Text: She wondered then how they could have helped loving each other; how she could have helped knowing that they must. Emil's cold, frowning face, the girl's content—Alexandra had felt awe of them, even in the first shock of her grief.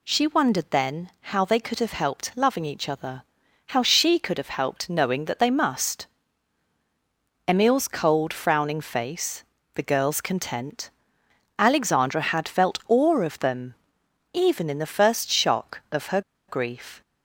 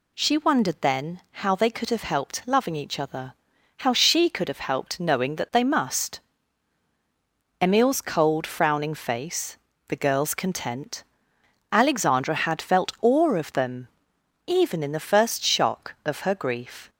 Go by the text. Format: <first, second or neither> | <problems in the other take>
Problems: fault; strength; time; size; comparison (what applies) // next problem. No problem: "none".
second | pauses between "her" and "grief"; slight; at 16.1 s; 0.28 s long